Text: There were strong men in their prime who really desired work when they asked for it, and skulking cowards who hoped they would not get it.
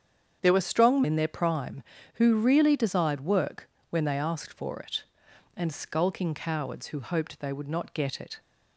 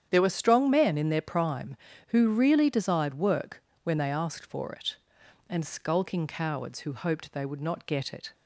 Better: second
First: starts louder than the rest; strong; until 1.4 s; 8 dB // skips "men"; at 1.0 s // pauses between "work" and "when"; slight; at 3.6 s; 0.22 s long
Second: starts louder than the rest; strong; until 1.1 s; 9 dB // pauses between "work" and "when"; slight; at 3.6 s; 0.22 s long

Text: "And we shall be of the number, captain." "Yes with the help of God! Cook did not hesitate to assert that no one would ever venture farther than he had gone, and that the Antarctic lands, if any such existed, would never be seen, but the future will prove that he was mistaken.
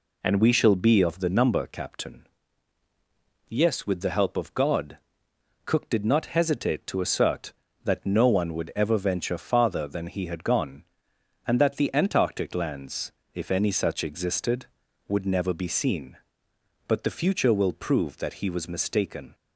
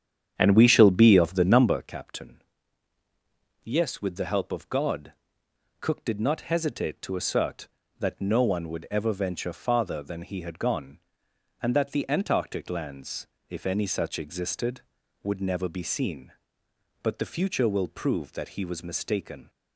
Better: first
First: none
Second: starts louder than the rest; strong; until 1.9 s; 8.5 dB

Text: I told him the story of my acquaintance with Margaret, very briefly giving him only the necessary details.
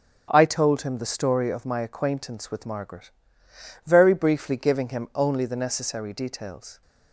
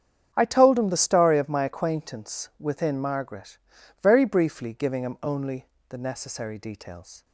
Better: first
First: starts louder than the rest; until 1.3 s; 7 dB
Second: starts louder than the rest; strong; until 1.3 s; 8.5 dB // says "within" for "with"; at 2.5 s // pauses between "only" and "the"; slight; at 5.6 s; 0.22 s long

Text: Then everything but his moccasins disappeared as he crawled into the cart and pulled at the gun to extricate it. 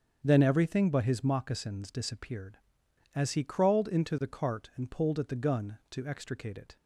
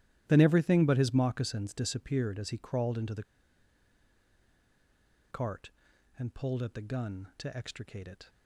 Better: first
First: starts louder than the rest; strong; until 1.2 s; 7.5 dB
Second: starts louder than the rest; strong; until 1.2 s; 13 dB // pauses between "the" and "cart"; strong; at 3.2 s; 2.0 s long

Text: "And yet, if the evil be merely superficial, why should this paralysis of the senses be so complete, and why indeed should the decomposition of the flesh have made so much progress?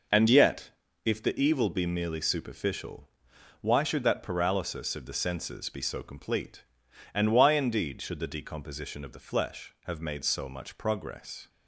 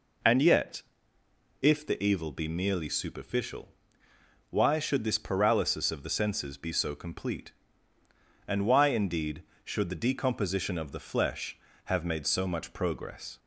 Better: second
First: says "that" for "this"; at 4.0 s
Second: none

